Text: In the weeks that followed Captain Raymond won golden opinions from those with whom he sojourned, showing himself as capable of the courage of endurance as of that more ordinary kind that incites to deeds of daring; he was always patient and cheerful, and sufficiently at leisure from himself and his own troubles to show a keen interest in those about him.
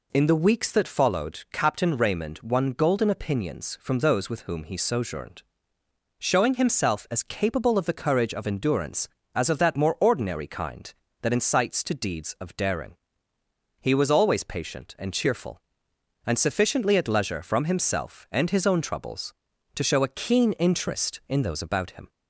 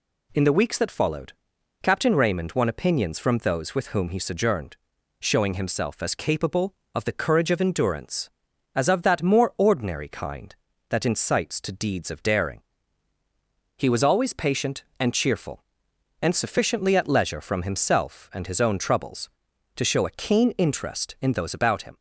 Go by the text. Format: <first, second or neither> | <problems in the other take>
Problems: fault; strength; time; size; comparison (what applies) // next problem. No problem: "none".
first | pauses between "followed" and "Captain"; noticeable; at 1.3 s; 0.50 s long // skips "golden"; at 2.6 s